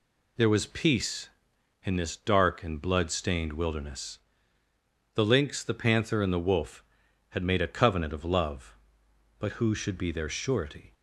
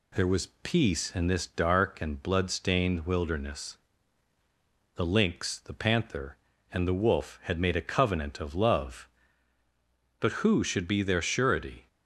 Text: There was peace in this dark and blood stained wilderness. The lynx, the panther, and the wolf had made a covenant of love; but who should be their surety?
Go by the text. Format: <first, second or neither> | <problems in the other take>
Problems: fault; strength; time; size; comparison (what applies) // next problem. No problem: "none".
neither | none